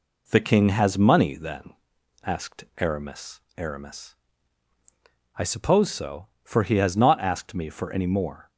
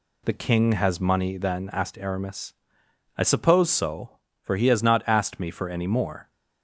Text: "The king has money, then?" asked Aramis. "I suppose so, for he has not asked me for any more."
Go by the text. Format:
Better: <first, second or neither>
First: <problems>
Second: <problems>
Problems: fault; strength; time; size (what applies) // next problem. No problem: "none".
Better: second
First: says "Aramis" twice; at 3.5 s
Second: none